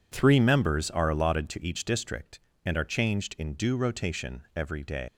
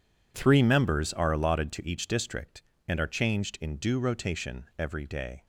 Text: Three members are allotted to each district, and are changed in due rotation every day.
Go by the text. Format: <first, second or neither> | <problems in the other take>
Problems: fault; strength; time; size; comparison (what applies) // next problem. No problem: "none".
second | leaves "day" unfinished; at 5.0 s; 145 ms